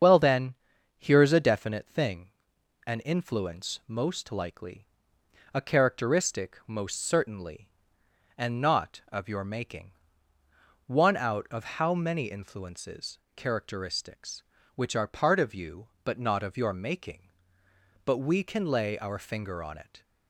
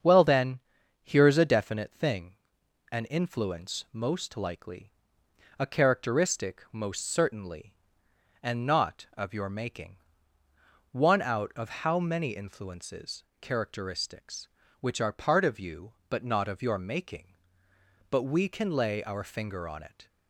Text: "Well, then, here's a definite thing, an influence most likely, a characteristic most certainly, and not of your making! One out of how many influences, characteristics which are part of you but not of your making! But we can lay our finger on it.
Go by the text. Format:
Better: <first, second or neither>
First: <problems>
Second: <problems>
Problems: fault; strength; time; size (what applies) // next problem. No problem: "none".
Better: second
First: loses the start of "Well"; at 0.0 s; 50 ms // starts louder than the rest; strong; until 1.4 s; 7 dB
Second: starts louder than the rest; strong; until 1.4 s; 7 dB